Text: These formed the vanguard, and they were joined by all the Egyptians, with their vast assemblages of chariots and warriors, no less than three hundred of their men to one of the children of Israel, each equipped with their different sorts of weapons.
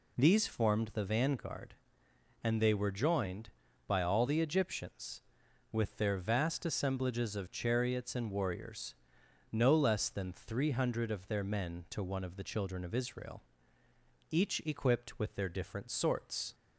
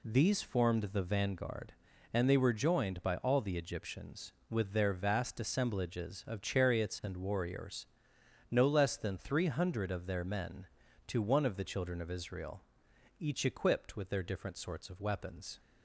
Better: second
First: stops before "of weapons"; at 16.5 s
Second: none

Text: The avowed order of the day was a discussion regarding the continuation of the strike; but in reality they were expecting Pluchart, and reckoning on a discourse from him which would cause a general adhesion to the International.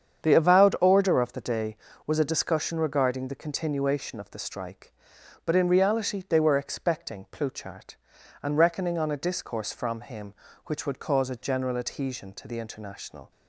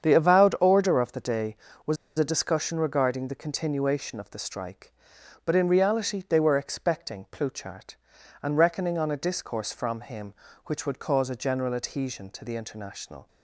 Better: first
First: starts louder than the rest; strong; until 1.3 s; 8 dB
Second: starts louder than the rest; strong; until 1.1 s; 8 dB // pauses between "was" and "a"; slight; at 1.9 s; 0.21 s long

